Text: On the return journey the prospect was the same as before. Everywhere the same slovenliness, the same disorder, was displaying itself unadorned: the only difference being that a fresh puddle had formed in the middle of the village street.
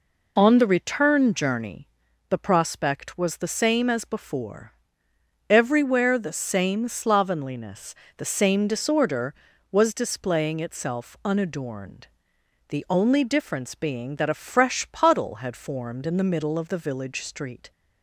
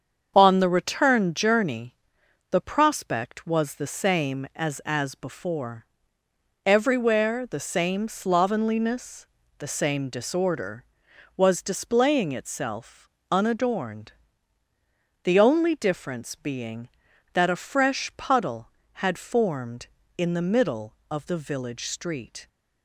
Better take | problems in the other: first | starts louder than the rest; strong; until 1.3 s; 7 dB // pauses between "journey" and "the"; noticeable; at 1.9 s; 0.56 s long; also in the first // says "as" twice; at 4.8 s // pauses between "itself" and "unadorned"; slight; at 13.1 s; 0.18 s long

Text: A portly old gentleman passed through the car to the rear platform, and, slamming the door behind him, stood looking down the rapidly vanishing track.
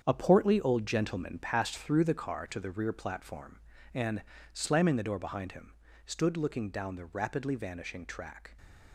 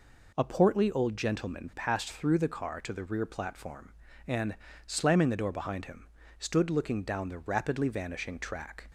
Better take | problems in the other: second | gets quieter; strong; throughout; 10 dB

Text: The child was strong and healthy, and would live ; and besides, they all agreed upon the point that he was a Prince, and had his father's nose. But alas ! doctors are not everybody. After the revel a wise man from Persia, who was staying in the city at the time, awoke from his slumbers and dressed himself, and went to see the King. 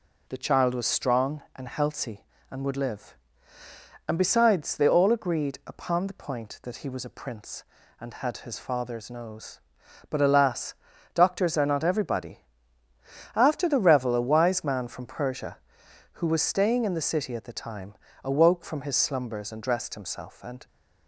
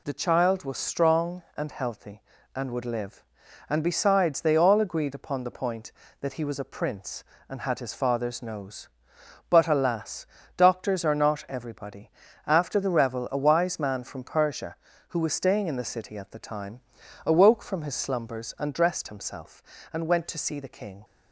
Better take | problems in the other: second | stops before "went to see the King"; at 20.6 s

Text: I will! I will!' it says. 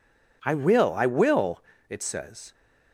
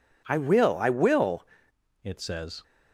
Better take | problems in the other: first | changes voice at "it"; from 2.0 s on; 0.6 s long

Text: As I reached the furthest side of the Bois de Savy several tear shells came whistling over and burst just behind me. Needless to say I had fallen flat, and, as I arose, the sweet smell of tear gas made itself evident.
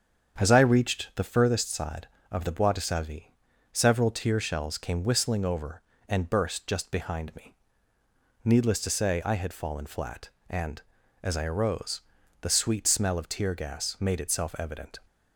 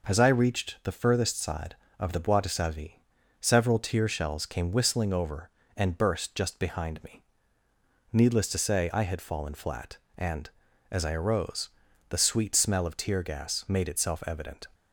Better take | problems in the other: second | starts louder than the rest; strong; until 1.6 s; 7.5 dB // pauses between "Savy" and "several"; at 3.3 s; 0.40 s long; also in the second

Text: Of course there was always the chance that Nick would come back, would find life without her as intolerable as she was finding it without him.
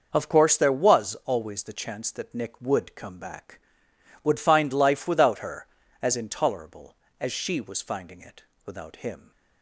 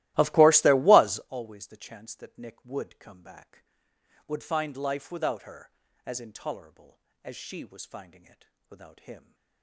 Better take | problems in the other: first | starts louder than the rest; strong; until 1.3 s; 16.5 dB // pauses between "it" and "without"; slight; at 8.4 s; 0.22 s long; slight in the first

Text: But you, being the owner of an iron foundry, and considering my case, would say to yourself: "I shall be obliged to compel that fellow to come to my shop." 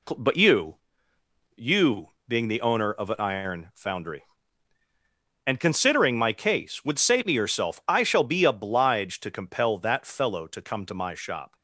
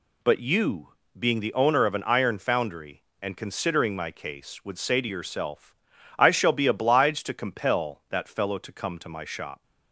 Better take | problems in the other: second | says "you" twice; at 1.5 s

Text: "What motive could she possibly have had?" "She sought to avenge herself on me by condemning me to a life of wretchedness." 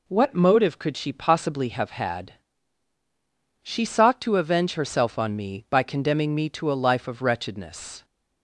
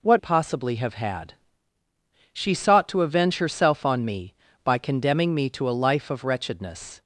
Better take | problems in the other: first | skips "motive could she"; at 0.1 s

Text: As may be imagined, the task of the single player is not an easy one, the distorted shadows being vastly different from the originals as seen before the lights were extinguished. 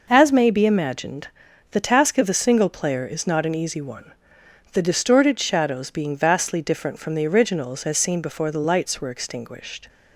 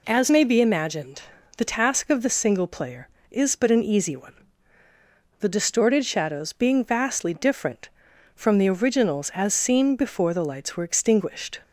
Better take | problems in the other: first | says "but" for "not"; at 3.5 s

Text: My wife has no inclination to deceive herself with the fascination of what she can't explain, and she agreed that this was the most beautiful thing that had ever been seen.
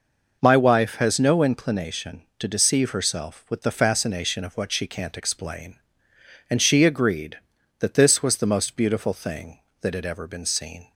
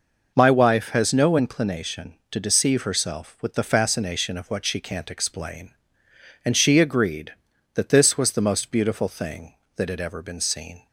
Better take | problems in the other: neither | none

